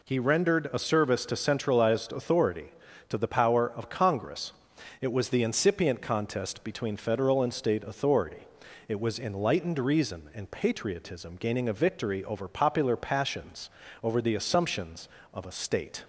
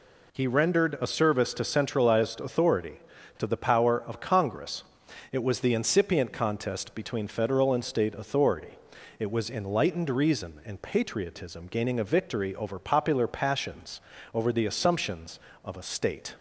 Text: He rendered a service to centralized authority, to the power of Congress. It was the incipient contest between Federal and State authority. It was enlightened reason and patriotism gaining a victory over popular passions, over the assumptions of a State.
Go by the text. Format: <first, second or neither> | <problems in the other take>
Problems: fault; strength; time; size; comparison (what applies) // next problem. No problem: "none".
neither | none